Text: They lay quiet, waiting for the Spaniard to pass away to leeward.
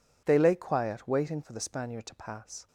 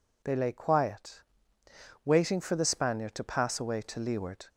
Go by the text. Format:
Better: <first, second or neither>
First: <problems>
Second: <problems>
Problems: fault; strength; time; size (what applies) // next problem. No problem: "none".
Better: second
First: stops before "away to leeward"; at 2.6 s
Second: none